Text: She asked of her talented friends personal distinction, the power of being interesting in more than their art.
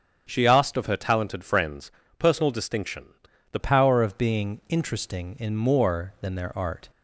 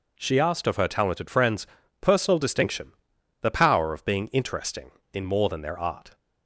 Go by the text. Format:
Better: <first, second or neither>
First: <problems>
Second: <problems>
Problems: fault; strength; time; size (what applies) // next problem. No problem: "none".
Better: second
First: starts louder than the rest; strong; until 1.2 s; 8 dB // pauses between "friends" and "personal"; slight; at 1.8 s; 0.28 s long // changes voice at "power"; from 3.5 s on; 3.3 s long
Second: pauses between "friends" and "personal"; slight; at 1.6 s; 0.34 s long